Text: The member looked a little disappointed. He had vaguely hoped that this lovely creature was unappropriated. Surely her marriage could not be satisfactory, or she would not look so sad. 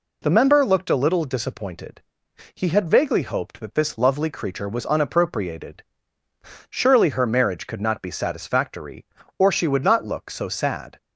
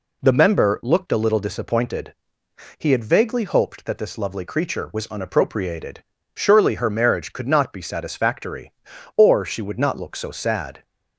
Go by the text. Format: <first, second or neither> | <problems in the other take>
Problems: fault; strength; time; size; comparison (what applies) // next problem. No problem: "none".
neither | none